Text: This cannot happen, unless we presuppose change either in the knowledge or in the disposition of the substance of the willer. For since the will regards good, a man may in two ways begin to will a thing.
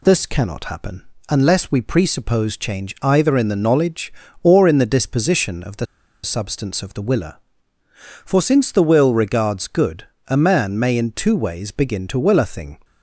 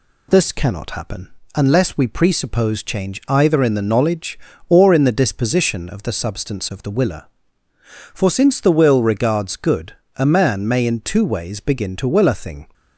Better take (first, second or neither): second